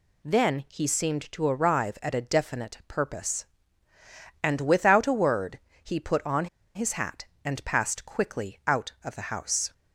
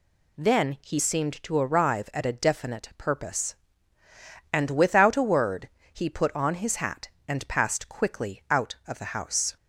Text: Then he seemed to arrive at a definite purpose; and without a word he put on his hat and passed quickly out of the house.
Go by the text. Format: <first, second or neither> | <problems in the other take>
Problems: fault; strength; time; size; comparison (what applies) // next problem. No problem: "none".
second | pauses between "word" and "he"; slight; at 5.5 s; 0.24 s long; slight in the second // pauses between "on" and "his"; slight; at 6.4 s; 0.28 s long